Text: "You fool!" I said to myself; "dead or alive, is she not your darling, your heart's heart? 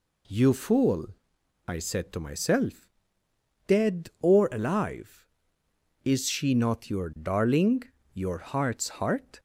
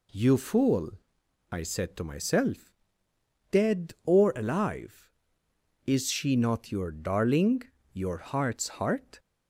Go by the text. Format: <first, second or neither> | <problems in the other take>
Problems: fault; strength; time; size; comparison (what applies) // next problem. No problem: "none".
neither | none